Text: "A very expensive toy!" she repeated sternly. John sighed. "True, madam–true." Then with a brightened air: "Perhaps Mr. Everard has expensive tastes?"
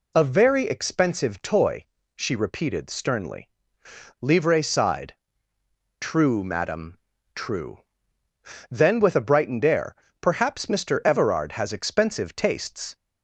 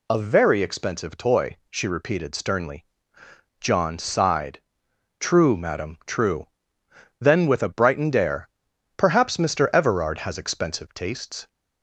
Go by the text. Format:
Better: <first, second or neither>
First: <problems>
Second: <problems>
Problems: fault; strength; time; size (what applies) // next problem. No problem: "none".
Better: second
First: says "Livre" for "John"; at 4.2 s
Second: none